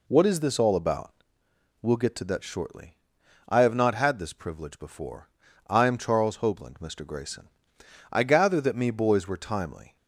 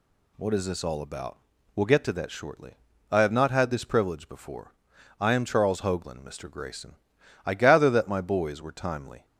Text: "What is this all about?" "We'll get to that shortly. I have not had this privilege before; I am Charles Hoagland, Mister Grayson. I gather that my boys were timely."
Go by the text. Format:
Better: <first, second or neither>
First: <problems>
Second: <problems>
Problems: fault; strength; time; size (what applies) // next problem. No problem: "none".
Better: second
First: says "me" for "my"; at 8.7 s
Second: none